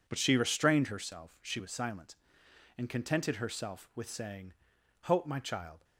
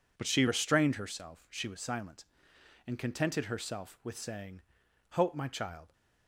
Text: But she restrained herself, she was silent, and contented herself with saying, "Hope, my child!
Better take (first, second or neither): neither